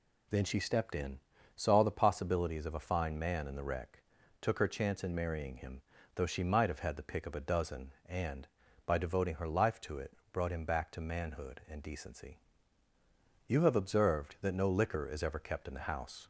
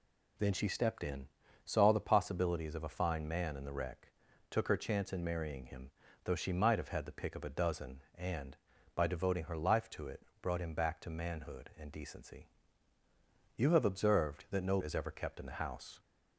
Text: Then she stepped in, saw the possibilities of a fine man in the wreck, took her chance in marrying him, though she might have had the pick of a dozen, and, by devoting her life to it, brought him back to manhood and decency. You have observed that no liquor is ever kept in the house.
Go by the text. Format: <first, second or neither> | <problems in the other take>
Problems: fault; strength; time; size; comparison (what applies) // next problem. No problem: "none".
first | skips "liquor"; at 14.7 s